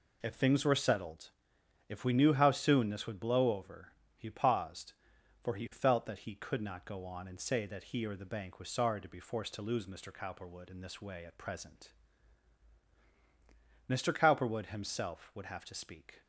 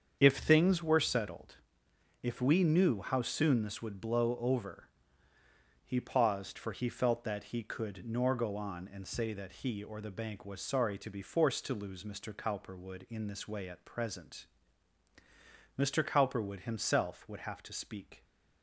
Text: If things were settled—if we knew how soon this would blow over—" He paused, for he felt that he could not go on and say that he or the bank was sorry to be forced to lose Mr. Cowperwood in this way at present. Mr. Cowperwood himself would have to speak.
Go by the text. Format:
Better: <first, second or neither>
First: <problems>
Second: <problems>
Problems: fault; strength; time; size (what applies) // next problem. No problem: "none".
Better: first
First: none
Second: starts louder than the rest; strong; until 1.2 s; 7.5 dB // says "nor" for "not"; at 8.0 s